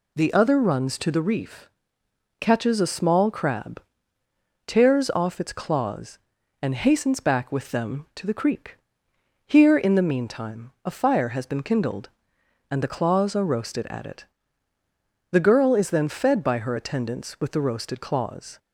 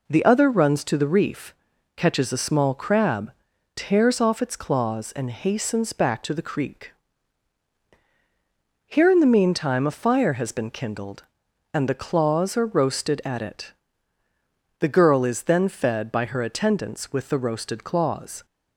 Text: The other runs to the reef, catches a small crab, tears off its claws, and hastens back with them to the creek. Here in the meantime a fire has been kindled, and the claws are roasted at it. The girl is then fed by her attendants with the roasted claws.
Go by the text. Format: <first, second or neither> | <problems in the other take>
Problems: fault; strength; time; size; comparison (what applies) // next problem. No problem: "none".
first | skips "with them"; at 6.2 s